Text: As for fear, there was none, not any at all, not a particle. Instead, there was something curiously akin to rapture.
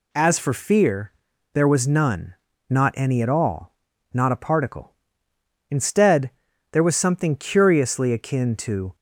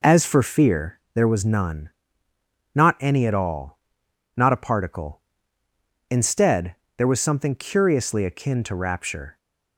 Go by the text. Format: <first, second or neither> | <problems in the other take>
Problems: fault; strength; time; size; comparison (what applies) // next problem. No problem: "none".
second | stops before "rapture"; at 8.9 s